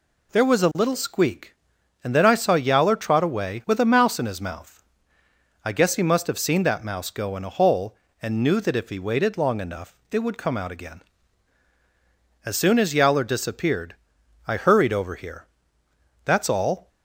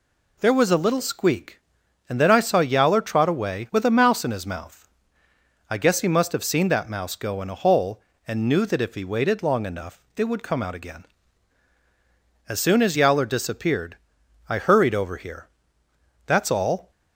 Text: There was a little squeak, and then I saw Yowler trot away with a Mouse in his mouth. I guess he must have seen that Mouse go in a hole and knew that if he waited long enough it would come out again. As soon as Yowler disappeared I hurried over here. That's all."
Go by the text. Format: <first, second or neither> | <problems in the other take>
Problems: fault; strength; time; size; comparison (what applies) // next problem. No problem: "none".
neither | pauses between "enough" and "it"; slight; the same in both // pauses between "disappeared" and "I"; noticeable; the same in both